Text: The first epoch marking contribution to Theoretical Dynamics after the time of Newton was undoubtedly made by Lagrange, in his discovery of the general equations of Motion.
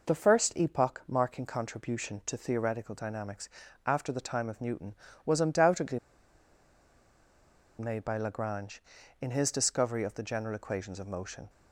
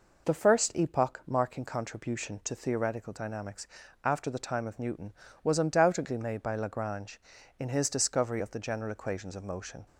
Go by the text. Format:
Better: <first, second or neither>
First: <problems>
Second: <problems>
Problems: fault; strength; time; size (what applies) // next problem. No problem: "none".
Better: second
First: pauses between "Dynamics" and "after"; at 3.4 s; 0.38 s long // pauses between "undoubtedly" and "made"; strong; at 5.9 s; 1.8 s long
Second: pauses between "Dynamics" and "after"; at 3.6 s; 0.38 s long